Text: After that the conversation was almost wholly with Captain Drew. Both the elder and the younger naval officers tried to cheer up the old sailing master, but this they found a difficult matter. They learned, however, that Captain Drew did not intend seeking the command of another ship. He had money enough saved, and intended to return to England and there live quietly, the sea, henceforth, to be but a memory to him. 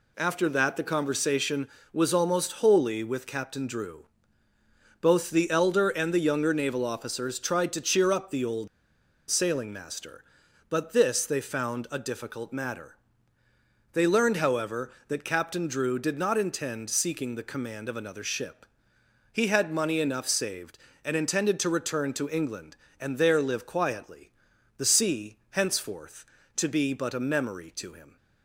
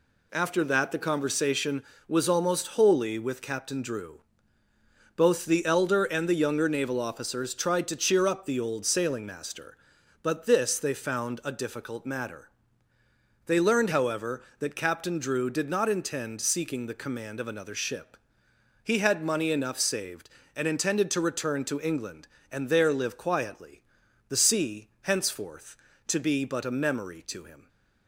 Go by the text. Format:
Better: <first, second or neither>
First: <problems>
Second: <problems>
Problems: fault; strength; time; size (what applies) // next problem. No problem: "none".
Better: second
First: pauses between "old" and "sailing"; noticeable; at 8.6 s; 0.62 s long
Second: none